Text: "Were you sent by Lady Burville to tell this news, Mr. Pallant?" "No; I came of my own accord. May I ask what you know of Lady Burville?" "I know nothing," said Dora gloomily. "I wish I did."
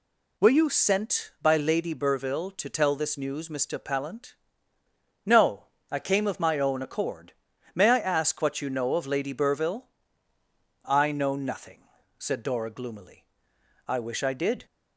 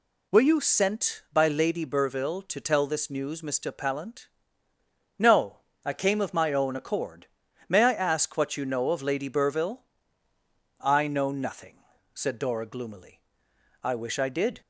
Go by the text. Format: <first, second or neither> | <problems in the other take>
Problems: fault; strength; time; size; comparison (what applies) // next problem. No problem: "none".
neither | none